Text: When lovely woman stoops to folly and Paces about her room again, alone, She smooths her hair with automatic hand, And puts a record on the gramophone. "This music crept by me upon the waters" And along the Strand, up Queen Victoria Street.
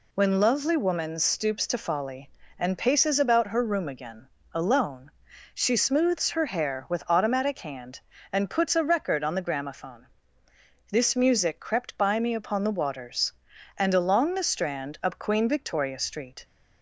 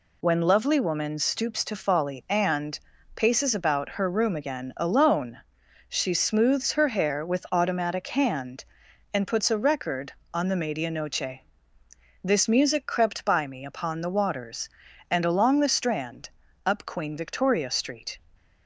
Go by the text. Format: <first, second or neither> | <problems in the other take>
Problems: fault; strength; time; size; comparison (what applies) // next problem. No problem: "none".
first | pauses between "and" and "Paces"; slight; at 2.7 s; 0.36 s long // says "medianoche" for "gramophone"; at 10.6 s